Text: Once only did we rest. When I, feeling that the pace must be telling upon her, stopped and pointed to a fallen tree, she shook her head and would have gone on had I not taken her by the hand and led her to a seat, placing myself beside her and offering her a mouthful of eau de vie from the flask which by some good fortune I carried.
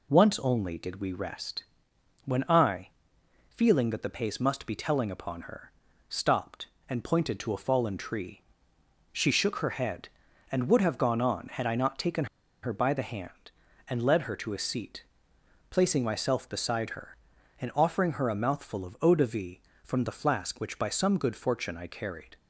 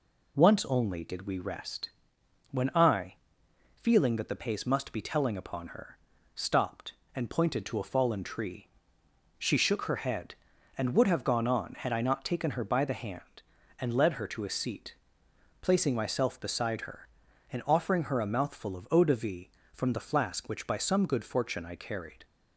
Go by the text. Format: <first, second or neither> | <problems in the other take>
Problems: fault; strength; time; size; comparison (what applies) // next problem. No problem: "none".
second | pauses between "taken" and "her"; at 12.2 s; 0.39 s long